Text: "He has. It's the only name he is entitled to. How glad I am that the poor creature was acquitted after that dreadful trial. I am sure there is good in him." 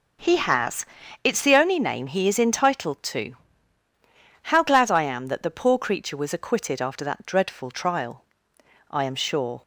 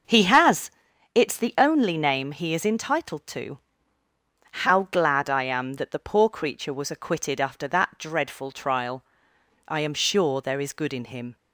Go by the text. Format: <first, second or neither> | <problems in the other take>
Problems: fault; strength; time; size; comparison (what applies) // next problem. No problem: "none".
second | stops before "there is good in him"; at 9.6 s